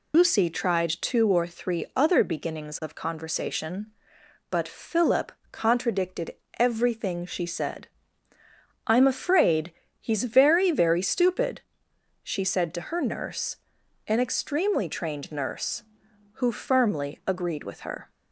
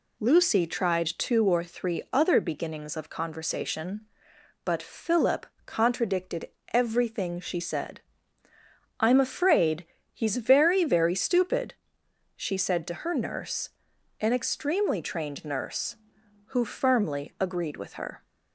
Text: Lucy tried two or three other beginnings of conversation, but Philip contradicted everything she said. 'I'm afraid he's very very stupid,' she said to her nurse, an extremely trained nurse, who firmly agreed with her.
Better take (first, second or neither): second